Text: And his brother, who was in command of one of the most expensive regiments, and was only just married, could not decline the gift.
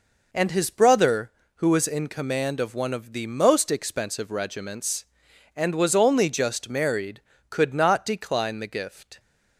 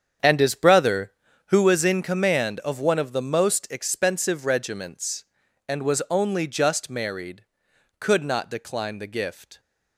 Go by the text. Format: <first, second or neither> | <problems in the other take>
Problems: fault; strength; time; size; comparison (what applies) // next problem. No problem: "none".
first | starts louder than the rest; strong; until 1.7 s; 8 dB